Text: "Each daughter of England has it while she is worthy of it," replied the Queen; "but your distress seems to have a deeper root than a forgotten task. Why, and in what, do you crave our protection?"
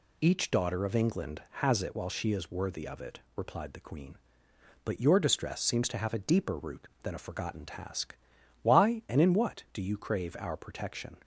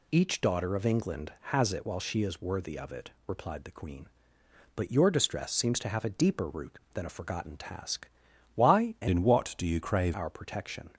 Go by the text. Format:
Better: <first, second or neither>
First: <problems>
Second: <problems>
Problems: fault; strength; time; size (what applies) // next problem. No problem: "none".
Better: first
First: none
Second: changes voice from "in" to "crave"; from 9.0 to 10.1 s; 1.1 s long